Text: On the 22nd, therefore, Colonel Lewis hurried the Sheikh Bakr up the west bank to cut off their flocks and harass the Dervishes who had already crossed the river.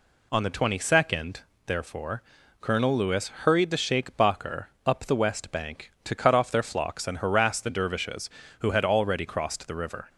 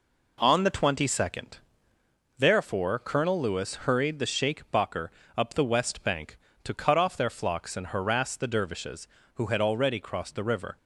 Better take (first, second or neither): first